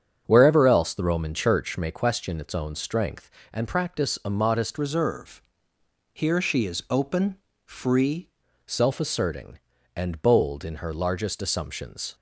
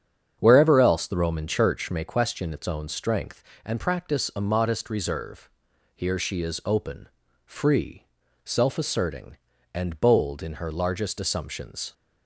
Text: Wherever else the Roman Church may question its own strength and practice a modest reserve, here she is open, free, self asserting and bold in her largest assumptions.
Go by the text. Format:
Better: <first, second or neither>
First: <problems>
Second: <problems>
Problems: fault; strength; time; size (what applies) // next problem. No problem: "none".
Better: second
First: starts louder than the rest; strong; until 1.2 s; 7.5 dB // changes voice from "reserve" to "free"; from 4.7 to 8.2 s; 3.5 s long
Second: starts louder than the rest; strong; until 1.4 s; 8 dB